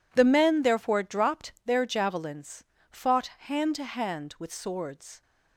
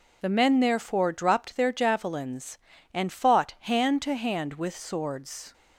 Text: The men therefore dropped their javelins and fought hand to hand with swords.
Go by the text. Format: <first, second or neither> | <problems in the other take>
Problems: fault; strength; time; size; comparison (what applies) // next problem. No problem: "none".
second | skips "and"; at 2.7 s // pauses between "fought" and "hand"; slight; at 3.2 s; 0.20 s long